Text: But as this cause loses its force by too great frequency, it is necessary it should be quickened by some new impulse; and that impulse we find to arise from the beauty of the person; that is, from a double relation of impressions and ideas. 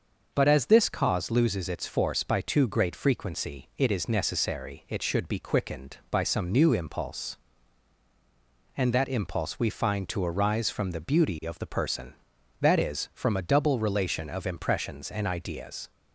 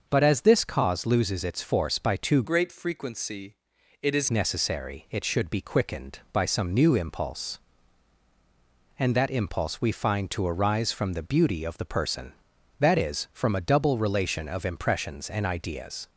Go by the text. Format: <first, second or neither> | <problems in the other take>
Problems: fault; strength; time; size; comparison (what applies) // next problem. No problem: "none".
first | starts louder than the rest; noticeable; until 1.1 s; 6 dB; noticeable in the first // changes voice from "great" to "is"; from 2.4 to 4.2 s; 1.8 s long